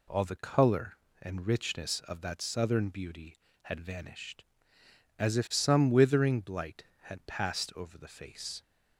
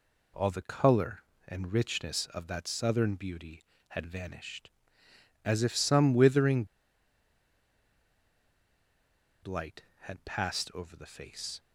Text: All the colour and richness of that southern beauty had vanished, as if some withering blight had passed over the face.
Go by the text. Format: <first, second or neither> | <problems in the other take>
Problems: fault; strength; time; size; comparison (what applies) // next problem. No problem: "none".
first | pauses between "withering" and "blight"; strong; at 6.6 s; 2.7 s long